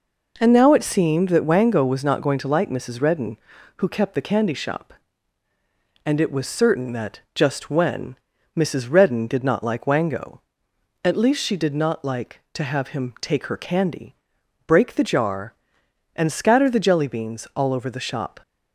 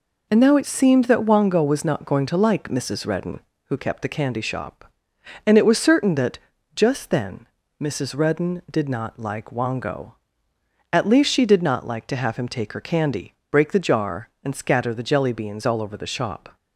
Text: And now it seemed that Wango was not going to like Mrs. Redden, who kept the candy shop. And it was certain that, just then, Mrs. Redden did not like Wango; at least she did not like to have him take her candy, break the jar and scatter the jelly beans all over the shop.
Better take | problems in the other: second | says "when" for "then"; at 7.7 s

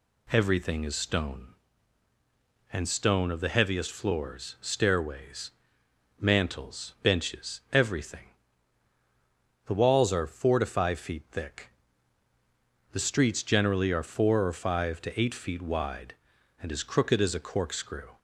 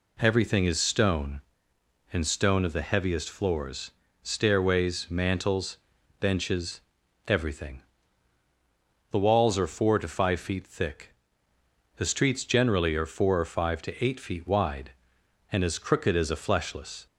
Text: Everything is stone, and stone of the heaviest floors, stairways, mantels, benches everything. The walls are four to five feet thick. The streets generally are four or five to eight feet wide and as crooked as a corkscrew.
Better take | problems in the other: first | pauses between "benches" and "everything"; noticeable; at 6.7 s; 0.48 s long // says "fleshless" for "corkscrew"; at 16.3 s

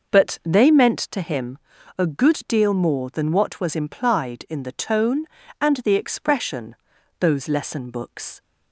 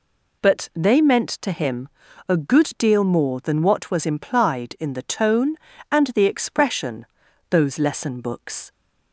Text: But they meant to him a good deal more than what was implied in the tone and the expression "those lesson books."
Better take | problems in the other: second | starts louder than the rest; noticeable; until 1.2 s; 6 dB // pauses between "him" and "a"; at 1.5 s; 0.38 s long; also in the second // pauses between "expression" and "those"; at 6.7 s; 0.44 s long; also in the second

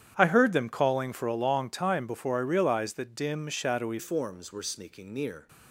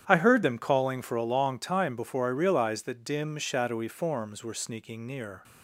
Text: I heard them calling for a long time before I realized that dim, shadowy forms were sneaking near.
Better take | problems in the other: second | starts louder than the rest; strong; until 1.1 s; 9.5 dB; strong in the second // changes voice at "forms"; from 3.9 s on; 1.5 s long

